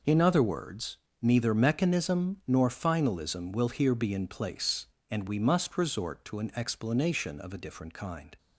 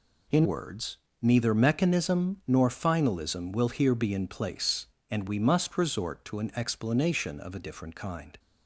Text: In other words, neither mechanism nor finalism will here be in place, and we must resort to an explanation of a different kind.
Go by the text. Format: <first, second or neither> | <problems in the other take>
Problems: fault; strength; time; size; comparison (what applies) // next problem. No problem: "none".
first | skips "other"; at 0.4 s